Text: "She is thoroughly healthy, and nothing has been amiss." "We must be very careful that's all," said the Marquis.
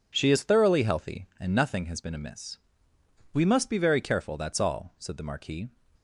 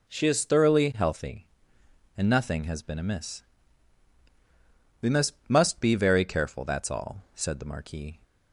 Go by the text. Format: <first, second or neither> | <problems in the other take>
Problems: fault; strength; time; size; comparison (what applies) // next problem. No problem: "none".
first | says "must" twice; at 5.4 s